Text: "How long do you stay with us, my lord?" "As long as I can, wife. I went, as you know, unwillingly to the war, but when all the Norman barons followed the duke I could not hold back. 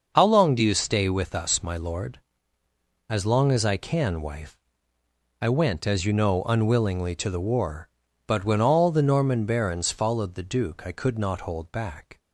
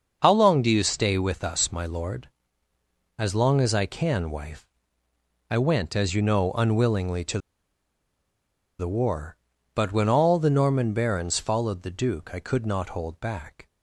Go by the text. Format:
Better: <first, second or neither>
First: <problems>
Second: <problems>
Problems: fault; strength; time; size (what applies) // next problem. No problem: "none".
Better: first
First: starts louder than the rest; until 1.1 s; 6 dB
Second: starts louder than the rest; until 1.2 s; 6 dB // pauses between "to" and "the"; strong; at 7.3 s; 1.4 s long